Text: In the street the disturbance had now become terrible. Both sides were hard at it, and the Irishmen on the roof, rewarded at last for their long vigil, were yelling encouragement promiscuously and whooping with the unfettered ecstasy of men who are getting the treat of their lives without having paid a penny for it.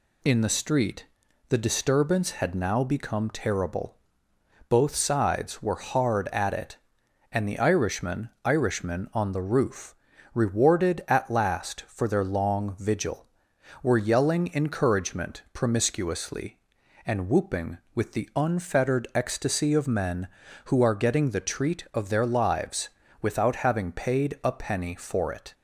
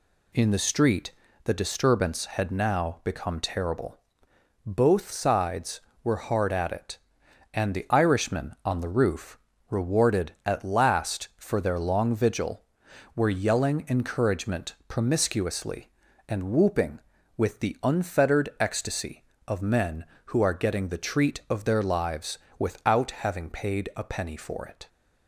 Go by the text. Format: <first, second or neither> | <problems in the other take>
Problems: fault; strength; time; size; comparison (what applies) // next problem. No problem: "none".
second | pauses between "street" and "the"; at 1.0 s; 0.44 s long; slight in the second // says "Irishmen" twice; at 8.4 s // pauses between "lives" and "without"; slight; at 22.8 s; 0.34 s long; slight in the second